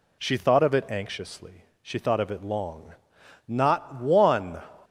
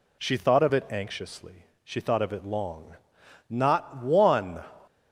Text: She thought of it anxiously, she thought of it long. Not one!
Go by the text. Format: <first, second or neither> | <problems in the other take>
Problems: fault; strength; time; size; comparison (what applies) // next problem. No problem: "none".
neither | none